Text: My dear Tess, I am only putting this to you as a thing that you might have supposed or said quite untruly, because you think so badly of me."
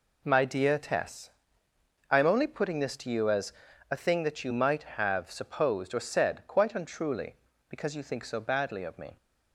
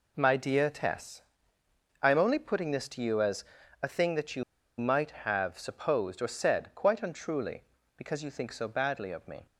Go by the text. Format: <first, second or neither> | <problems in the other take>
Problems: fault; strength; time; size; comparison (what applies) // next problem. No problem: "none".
first | pauses between "as" and "a"; at 3.4 s; 0.38 s long; also in the first // pauses between "you" and "might"; at 4.4 s; 0.36 s long